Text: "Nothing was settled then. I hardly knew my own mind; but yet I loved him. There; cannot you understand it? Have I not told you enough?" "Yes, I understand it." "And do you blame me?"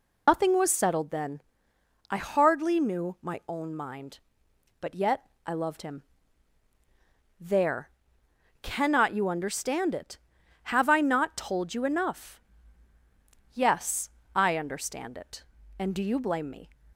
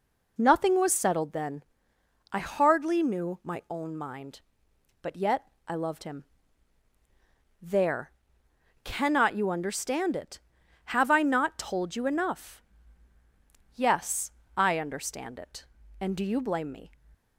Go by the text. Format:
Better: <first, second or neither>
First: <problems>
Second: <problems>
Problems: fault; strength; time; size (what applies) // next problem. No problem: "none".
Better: second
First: loses the start of "Nothing"; at 0.2 s; 125 ms // pauses between "yet" and "I"; slight; at 5.2 s; 0.18 s long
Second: pauses between "yet" and "I"; slight; at 5.4 s; 0.18 s long